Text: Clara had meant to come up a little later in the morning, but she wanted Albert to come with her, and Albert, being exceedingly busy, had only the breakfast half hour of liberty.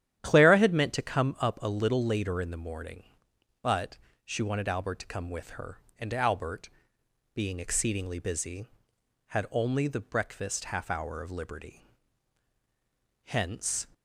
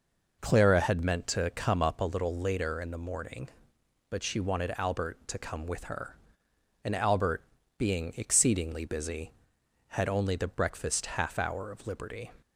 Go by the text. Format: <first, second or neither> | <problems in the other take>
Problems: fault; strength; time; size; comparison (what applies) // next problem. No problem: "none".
second | starts louder than the rest; strong; until 1.2 s; 11 dB // pauses between "but" and "she"; slight; at 3.9 s; 0.28 s long // goes on to say "Hence"; noticeable; from 13.2 s on; 0.64 s long